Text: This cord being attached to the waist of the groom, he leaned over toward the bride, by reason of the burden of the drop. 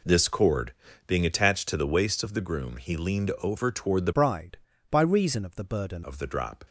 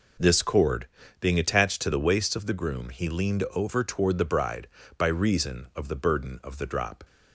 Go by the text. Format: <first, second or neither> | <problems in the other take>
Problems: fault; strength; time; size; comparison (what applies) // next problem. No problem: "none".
second | pauses between "cord" and "being"; slight; at 0.7 s; 0.34 s long; slight in the second // changes voice from "bride" to "burden"; from 4.1 to 6.0 s; 1.9 s long